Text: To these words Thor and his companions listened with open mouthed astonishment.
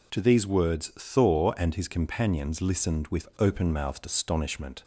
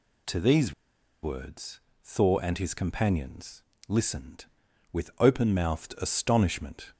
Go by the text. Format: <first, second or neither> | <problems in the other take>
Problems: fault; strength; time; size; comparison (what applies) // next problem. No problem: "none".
first | pauses between "these" and "words"; noticeable; at 0.7 s; 0.50 s long // pauses between "words" and "Thor"; slight; at 1.7 s; 0.22 s long // pauses between "companions" and "listened"; slight; at 3.6 s; 0.26 s long